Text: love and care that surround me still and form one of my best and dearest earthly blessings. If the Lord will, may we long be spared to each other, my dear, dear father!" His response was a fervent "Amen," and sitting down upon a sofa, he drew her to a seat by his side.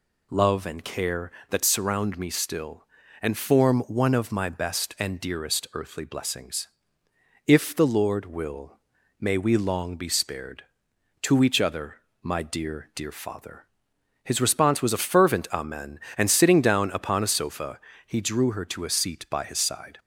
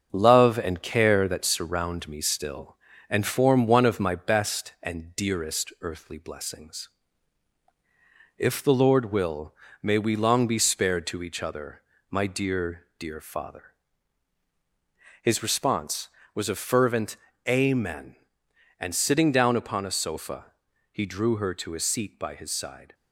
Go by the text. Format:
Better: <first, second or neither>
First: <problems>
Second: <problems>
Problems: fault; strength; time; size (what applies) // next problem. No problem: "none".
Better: first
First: none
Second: gets quieter; throughout; 3.5 dB // pauses between "fervent" and "Amen"; slight; at 17.1 s; 0.32 s long